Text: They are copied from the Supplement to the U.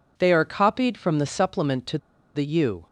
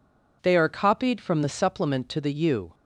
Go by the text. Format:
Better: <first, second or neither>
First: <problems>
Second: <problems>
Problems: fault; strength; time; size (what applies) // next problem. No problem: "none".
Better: second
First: pauses between "to" and "the"; at 1.9 s; 0.37 s long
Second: none